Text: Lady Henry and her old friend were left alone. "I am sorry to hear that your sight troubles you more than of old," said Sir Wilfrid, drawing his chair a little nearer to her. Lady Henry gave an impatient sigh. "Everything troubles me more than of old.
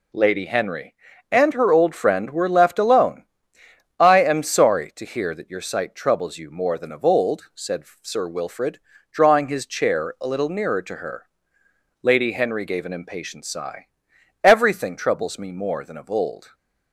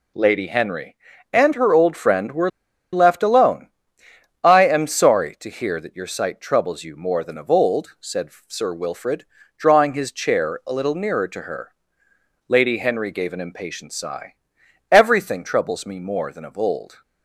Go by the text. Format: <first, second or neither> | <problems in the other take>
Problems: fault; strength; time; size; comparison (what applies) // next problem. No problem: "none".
first | pauses between "were" and "left"; at 2.4 s; 0.43 s long // pauses between "said" and "Sir"; slight; at 8.3 s; 0.16 s long; slight in the first